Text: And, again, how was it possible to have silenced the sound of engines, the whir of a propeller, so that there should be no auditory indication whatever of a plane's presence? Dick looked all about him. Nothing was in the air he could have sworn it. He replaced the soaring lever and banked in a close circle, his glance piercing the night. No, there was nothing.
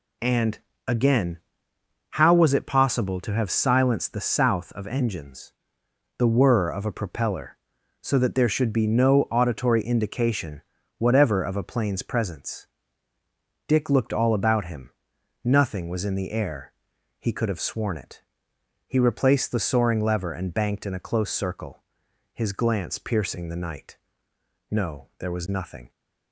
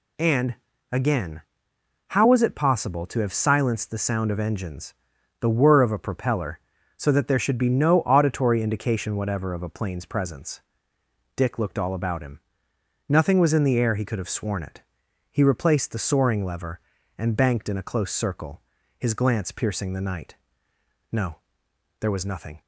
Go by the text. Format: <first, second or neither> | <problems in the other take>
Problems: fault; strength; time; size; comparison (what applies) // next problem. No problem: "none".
second | says "south" for "sound"; at 4.2 s // pauses between "indication" and "whatever"; slight; at 10.6 s; 0.36 s long // pauses between "air" and "he"; noticeable; at 16.7 s; 0.48 s long